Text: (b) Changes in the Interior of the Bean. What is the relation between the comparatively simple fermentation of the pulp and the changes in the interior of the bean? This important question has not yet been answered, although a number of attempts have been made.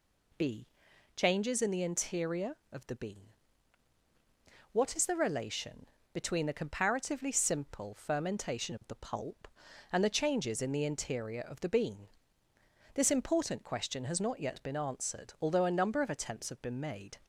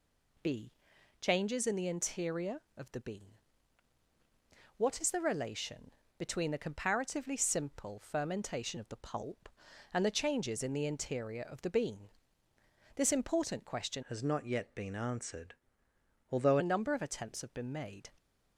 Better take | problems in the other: first | pauses between "relation" and "between"; slight; at 5.9 s; 0.26 s long; slight in the first // changes voice from "has" to "although"; from 14.0 to 16.5 s; 2.5 s long

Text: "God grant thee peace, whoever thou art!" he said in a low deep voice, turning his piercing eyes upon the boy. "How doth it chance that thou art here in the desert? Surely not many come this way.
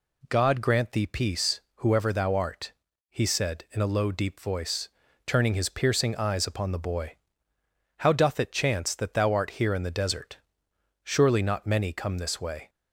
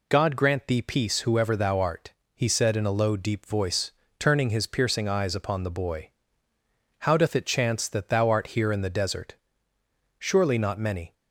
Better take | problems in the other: first | stops before "come this way"; at 11.1 s

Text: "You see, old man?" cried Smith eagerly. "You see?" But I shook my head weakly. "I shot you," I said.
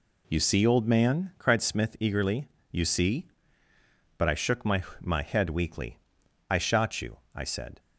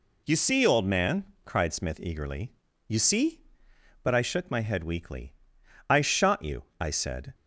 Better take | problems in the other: second | says "my" twice; at 4.9 s

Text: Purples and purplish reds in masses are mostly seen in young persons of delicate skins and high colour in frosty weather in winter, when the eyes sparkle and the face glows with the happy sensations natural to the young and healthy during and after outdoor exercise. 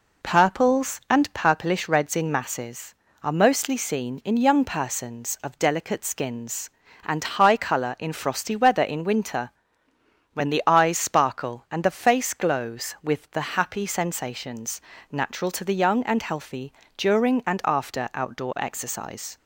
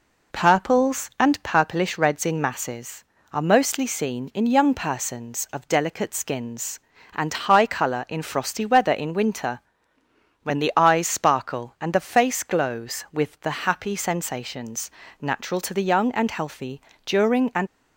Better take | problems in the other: first | pauses between "sensations" and "natural"; slight; at 14.8 s; 0.30 s long; slight in the first // pauses between "healthy" and "during"; slight; at 16.8 s; 0.24 s long; slight in the first // stops before "after outdoor exercise"; at 17.6 s

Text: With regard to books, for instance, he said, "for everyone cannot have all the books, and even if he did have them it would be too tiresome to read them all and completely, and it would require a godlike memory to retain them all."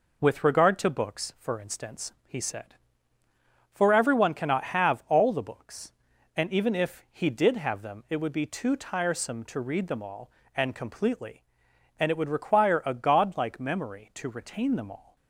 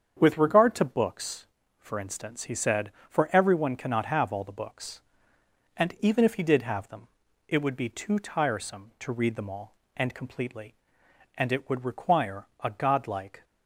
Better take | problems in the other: first | starts louder than the rest; strong; until 1.2 s; 7.5 dB // pauses between "them" and "it"; at 7.0 s; 0.42 s long // pauses between "require" and "a"; slight; at 12.4 s; 0.16 s long // stops before "memory to retain them all"; at 13.4 s

